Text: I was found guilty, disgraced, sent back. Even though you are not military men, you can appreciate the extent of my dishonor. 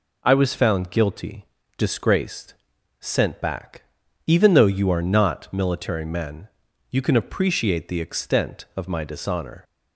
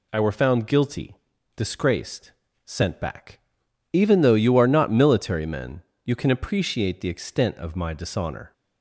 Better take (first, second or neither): first